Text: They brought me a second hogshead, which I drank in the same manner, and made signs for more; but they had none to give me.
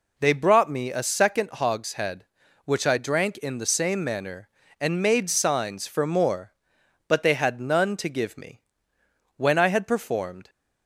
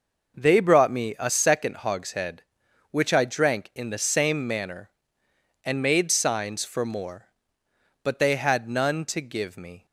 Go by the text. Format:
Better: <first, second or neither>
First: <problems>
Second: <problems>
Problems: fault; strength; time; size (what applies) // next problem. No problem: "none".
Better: second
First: goes on to say "When I had performed"; noticeable; from 9.3 s on; 1.1 s long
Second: none